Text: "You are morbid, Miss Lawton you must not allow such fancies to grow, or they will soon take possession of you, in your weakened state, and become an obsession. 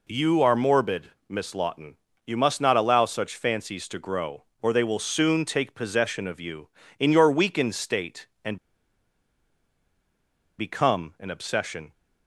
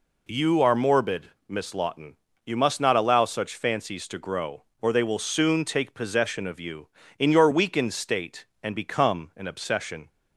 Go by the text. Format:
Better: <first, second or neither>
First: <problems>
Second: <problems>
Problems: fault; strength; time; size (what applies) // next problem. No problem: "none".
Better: second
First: pauses between "Lawton" and "you"; slight; at 1.9 s; 0.28 s long // pauses between "and" and "become"; strong; at 8.5 s; 2.0 s long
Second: pauses between "Lawton" and "you"; slight; at 2.1 s; 0.28 s long